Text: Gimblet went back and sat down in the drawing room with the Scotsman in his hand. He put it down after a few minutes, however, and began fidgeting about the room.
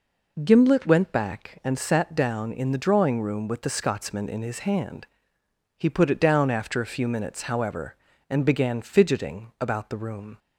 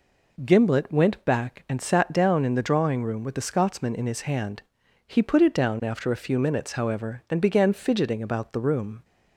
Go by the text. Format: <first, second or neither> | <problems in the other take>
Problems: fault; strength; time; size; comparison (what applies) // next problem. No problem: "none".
neither | none